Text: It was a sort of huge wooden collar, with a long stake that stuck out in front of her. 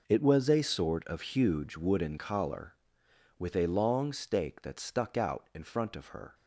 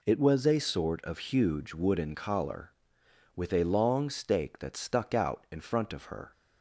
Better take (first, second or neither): second